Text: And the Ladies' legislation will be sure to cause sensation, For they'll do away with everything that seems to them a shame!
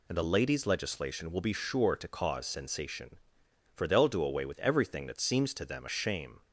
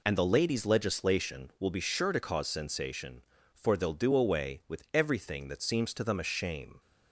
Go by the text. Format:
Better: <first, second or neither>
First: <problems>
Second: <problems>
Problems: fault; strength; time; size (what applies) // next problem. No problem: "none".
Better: neither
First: none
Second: none